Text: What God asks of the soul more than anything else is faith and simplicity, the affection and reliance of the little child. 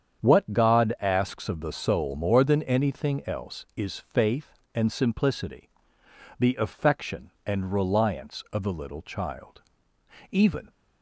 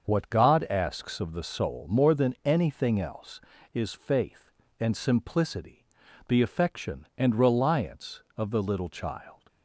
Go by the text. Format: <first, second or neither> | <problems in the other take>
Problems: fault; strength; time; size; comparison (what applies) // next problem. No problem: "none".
second | starts louder than the rest; strong; until 1.3 s; 8 dB; also in the second // goes on to say "Even"; slight; from 10.2 s on; 0.40 s long